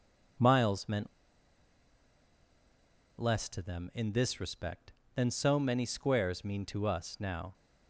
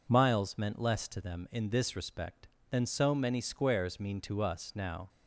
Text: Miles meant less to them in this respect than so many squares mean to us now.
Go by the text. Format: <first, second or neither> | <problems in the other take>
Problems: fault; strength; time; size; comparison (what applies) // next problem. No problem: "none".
second | pauses between "meant" and "less"; strong; at 1.0 s; 2.1 s long